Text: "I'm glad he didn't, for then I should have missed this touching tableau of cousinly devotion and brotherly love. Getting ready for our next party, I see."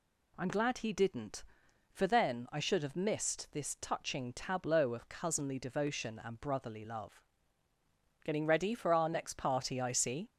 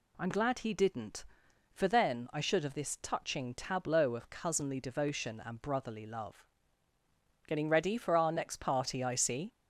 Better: first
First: none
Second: skips "missed"; at 2.7 s

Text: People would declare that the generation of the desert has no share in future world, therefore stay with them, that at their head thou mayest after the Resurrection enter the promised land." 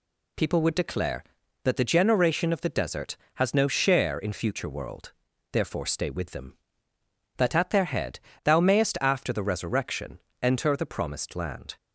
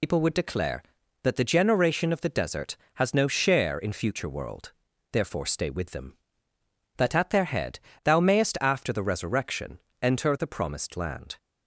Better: first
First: pauses between "head" and "thou"; slight; at 8.1 s; 0.24 s long // pauses between "Resurrection" and "enter"; slight; at 10.1 s; 0.24 s long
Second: loses the start of "People"; at 0.0 s; 65 ms // pauses between "head" and "thou"; slight; at 7.7 s; 0.24 s long // pauses between "Resurrection" and "enter"; slight; at 9.7 s; 0.24 s long

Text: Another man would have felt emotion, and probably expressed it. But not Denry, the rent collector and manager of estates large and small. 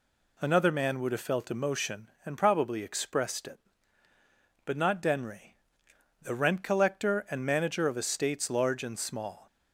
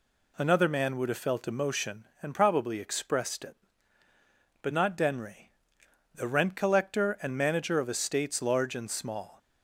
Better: neither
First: none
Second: none

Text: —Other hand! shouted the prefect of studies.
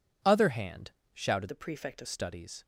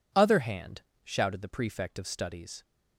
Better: second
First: changes voice from "the" to "of"; from 1.4 to 2.0 s; 0.6 s long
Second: none

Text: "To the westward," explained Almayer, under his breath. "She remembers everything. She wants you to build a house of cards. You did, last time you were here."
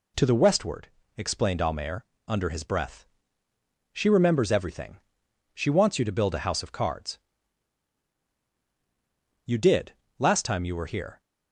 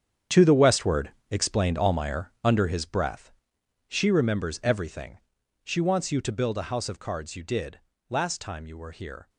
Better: first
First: none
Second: gets quieter; strong; throughout; 12.5 dB

